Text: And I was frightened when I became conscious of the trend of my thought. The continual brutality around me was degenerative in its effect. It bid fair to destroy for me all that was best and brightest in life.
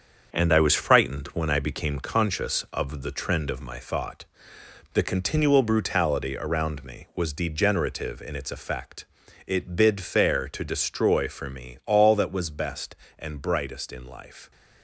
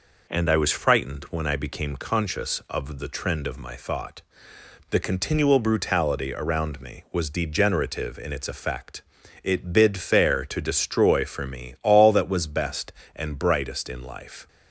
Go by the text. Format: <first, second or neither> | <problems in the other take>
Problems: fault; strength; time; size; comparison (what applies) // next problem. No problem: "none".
second | gets quieter; throughout; 6 dB